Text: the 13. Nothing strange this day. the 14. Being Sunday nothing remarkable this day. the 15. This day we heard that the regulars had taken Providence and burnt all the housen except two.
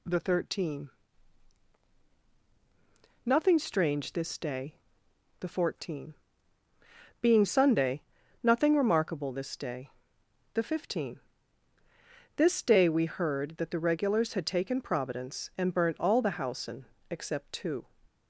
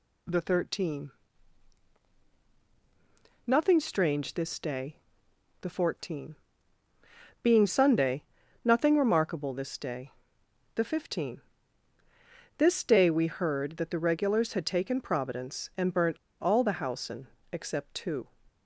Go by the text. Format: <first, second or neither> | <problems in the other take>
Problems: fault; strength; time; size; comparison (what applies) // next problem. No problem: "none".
first | pauses between "Sunday" and "nothing"; at 8.2 s; 0.38 s long; also in the first // pauses between "burnt" and "all"; slight; at 16.1 s; 0.26 s long // pauses between "housen" and "except"; slight; at 17.2 s; 0.24 s long; slight in the first